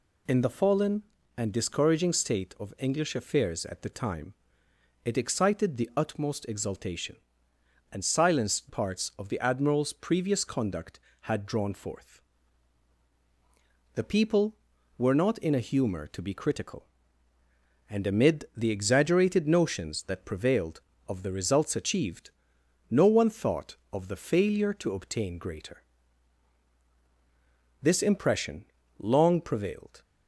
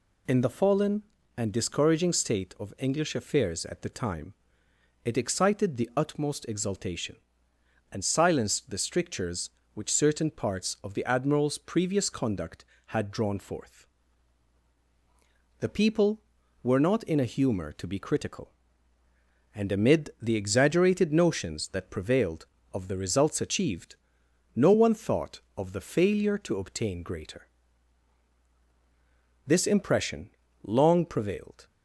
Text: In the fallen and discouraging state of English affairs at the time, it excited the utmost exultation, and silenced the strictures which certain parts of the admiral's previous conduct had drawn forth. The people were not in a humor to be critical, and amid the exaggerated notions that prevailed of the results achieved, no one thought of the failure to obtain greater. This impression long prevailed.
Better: second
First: skips "the strictures which certain"; at 8.6 s // pauses between "impression" and "long"; slight; at 28.6 s; 0.32 s long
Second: pauses between "impression" and "long"; slight; at 30.3 s; 0.32 s long

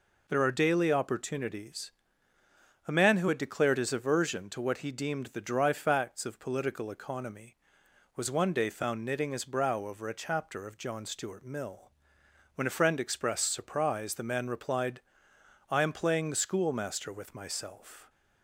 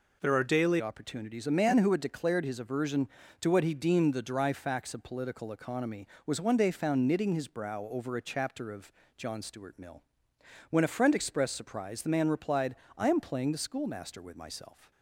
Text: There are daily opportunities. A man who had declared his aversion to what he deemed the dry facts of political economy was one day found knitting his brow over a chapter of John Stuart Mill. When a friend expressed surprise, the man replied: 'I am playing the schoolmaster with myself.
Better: first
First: none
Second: changes voice at "opportunities"; from 0.8 s on; 14.1 s long // pauses between "of" and "John"; slight; at 8.9 s; 0.26 s long

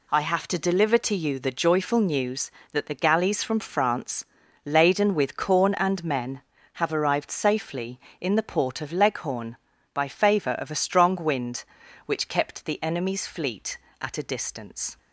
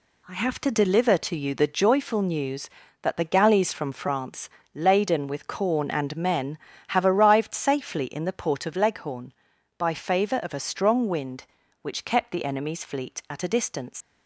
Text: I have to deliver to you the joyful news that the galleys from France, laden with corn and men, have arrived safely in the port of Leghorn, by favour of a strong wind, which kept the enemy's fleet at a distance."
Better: first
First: none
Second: leaves "distance" unfinished; at 14.0 s; 115 ms

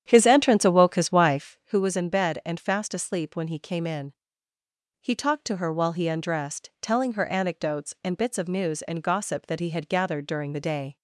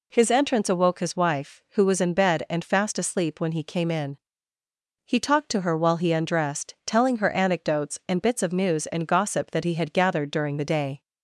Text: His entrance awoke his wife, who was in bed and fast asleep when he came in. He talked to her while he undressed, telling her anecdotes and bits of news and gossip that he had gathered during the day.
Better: second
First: starts louder than the rest; strong; until 1.7 s; 9.5 dB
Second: none

